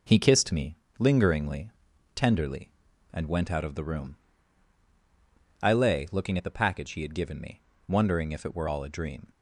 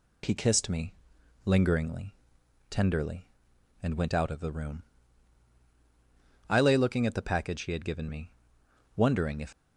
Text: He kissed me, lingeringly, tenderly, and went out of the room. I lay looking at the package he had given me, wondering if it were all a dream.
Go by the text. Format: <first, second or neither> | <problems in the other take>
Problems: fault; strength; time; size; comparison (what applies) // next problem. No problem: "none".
first | stops before "it were all a dream"; at 9.5 s